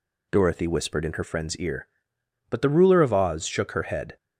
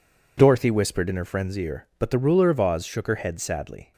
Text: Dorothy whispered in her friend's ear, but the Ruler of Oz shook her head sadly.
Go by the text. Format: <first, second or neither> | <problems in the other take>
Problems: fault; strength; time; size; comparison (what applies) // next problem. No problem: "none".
second | stops before "sadly"; at 4.1 s